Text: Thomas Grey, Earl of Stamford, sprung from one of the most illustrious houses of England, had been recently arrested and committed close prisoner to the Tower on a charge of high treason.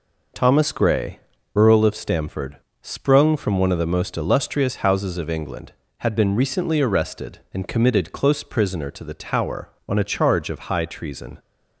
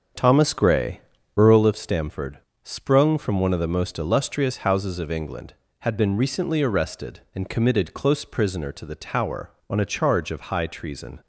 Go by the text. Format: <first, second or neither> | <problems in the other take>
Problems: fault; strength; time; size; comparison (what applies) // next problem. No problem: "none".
first | starts louder than the rest; strong; until 1.8 s; 7 dB